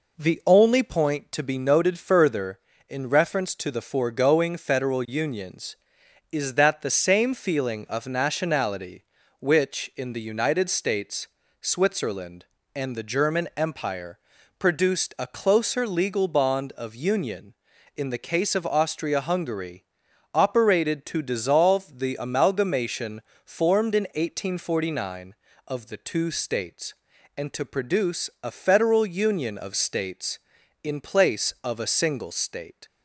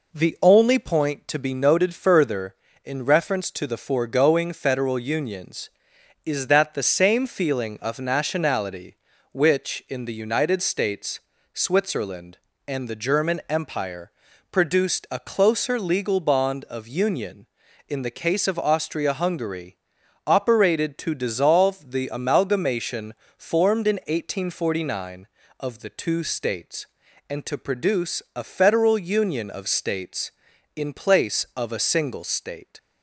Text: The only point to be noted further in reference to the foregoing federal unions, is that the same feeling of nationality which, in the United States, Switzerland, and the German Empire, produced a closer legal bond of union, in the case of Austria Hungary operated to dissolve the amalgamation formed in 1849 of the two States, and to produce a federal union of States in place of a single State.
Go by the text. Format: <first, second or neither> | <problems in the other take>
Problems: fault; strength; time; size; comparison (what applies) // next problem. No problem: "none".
neither | pauses between "Hungary" and "operated"; noticeable; the same in both // pauses between "amalgamation" and "formed"; slight; the same in both